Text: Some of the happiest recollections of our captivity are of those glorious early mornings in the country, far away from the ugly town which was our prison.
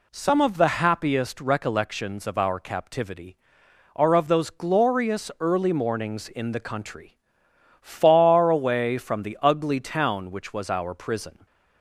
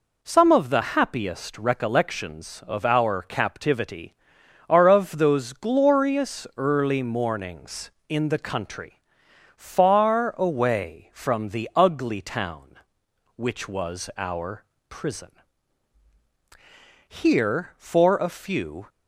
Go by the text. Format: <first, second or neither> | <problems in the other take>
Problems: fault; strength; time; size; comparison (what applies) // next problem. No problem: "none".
first | pauses between "our" and "prison"; slight; at 14.6 s; 0.24 s long // goes on to say "Here for a few"; from 17.2 s on; 1.6 s long